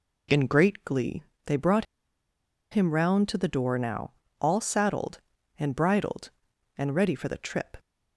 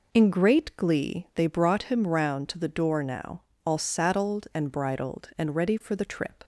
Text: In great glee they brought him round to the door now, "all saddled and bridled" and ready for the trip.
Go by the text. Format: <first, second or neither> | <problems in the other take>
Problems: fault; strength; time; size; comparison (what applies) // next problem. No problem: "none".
second | pauses between "glee" and "they"; slight; at 1.2 s; 0.22 s long // pauses between "brought" and "him"; noticeable; at 1.8 s; 0.86 s long